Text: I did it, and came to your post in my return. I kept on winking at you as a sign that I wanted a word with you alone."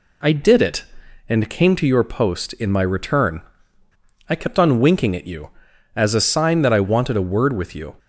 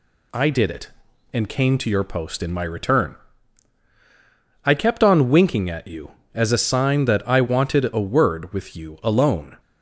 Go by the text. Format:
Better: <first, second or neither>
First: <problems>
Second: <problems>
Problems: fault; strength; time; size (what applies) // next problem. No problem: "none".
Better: second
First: stops before "alone"; at 7.9 s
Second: none